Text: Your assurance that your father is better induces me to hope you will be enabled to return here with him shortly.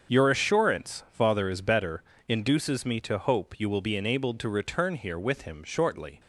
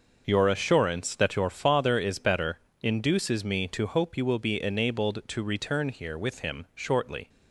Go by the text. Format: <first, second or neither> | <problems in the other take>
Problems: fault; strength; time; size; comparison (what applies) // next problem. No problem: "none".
second | starts louder than the rest; until 1.1 s; 6.5 dB; noticeable in the second // skips "that your"; at 1.0 s // pauses between "better" and "induces"; slight; at 2.0 s; 0.26 s long; slight in the second